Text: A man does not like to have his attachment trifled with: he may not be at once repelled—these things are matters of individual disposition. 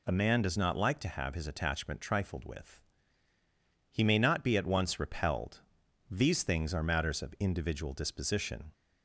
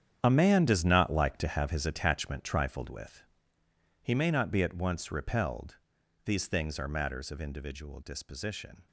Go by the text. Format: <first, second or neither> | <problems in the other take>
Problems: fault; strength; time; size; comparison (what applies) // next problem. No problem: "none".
first | gets quieter; strong; throughout; 13.5 dB